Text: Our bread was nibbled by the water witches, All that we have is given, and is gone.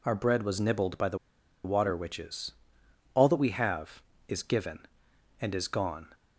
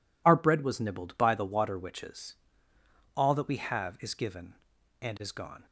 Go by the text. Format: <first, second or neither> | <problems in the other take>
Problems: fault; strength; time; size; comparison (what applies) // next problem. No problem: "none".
second | pauses between "the" and "water"; noticeable; at 1.1 s; 0.48 s long